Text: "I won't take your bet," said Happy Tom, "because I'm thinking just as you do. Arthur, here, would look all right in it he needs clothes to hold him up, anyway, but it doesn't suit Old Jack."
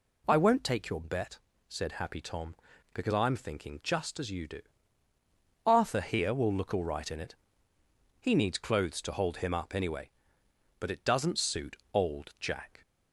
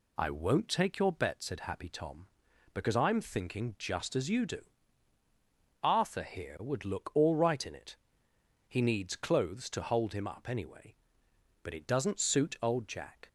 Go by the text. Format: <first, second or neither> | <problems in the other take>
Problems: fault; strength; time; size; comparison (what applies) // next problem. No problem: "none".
second | says "will" for "would"; at 6.3 s // pauses between "it" and "he"; noticeable; at 7.3 s; 0.86 s long; noticeable in the second // pauses between "suit" and "Old"; slight; at 11.7 s; 0.16 s long